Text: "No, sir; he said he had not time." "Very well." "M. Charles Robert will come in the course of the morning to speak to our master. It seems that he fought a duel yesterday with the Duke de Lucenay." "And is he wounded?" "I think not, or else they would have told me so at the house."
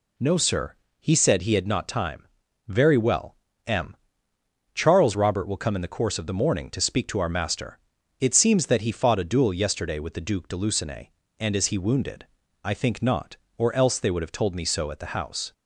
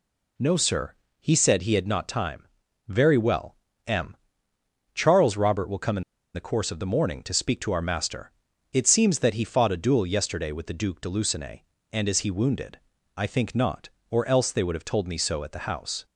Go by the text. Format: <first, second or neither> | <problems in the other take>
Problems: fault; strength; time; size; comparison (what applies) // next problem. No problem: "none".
first | pauses between "in" and "the"; slight; at 6.0 s; 0.32 s long